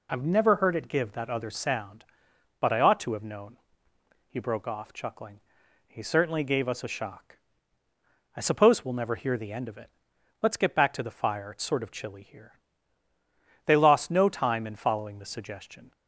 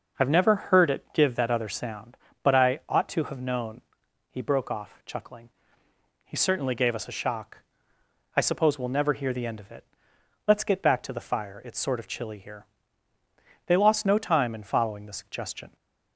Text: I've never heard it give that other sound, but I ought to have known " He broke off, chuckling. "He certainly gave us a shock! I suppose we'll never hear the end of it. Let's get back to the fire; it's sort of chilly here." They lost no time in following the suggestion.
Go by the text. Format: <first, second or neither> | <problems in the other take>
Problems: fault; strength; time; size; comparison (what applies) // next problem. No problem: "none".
neither | none